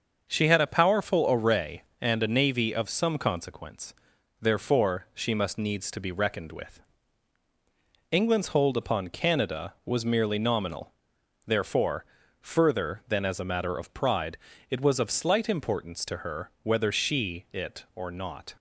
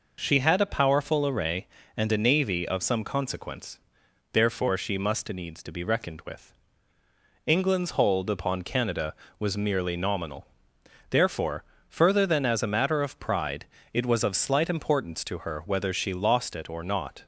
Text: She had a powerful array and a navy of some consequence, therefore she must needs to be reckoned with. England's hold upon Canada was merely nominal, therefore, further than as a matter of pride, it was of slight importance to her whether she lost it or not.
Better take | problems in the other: second | starts louder than the rest; until 1.3 s; 6.5 dB // skips "lost"; at 17.4 s

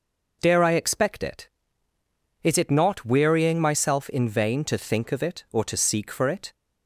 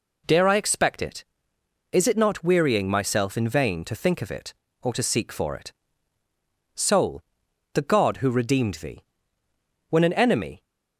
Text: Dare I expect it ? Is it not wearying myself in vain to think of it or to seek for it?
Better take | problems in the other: first | goes on to say "Soul the God who redeemed thee when an enemy"; strong; from 6.7 s on; 3.8 s long

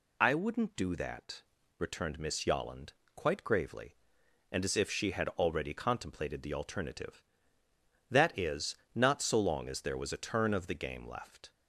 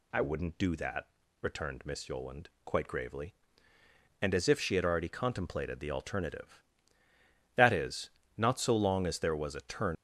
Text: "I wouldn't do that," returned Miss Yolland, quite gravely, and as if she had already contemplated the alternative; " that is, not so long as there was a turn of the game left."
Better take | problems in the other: first | stops before "of the game left"; at 9.9 s

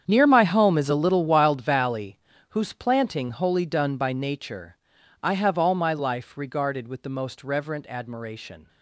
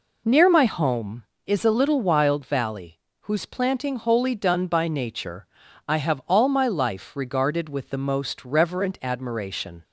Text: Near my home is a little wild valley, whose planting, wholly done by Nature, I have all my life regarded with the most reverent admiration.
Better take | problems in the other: second | gets quieter; strong; throughout; 15 dB

